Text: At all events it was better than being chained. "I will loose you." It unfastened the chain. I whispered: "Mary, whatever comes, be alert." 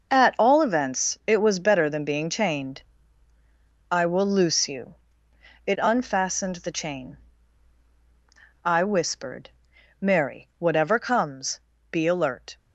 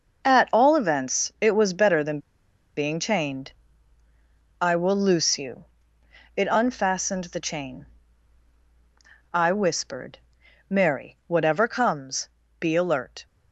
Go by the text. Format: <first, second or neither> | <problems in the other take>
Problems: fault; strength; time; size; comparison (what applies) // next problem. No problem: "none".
first | pauses between "than" and "being"; noticeable; at 2.1 s; 0.57 s long